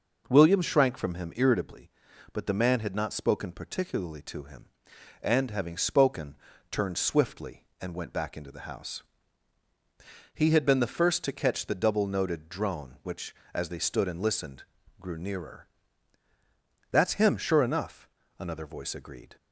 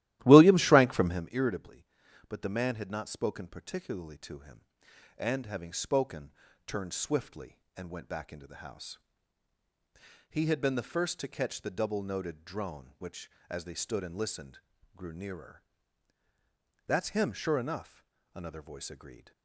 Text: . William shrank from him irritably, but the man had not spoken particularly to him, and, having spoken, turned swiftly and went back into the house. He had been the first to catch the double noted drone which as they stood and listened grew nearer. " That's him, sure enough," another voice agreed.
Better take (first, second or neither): first